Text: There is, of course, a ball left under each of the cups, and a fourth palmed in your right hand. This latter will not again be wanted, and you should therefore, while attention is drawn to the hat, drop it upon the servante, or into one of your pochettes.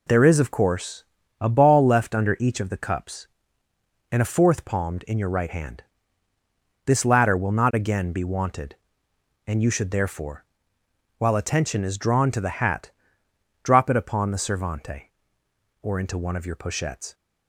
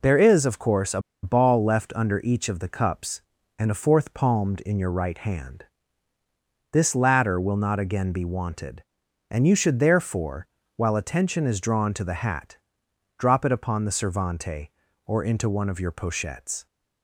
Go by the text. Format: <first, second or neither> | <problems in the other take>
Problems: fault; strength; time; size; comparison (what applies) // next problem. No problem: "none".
first | pauses between "a" and "ball"; slight; at 1.0 s; 0.22 s long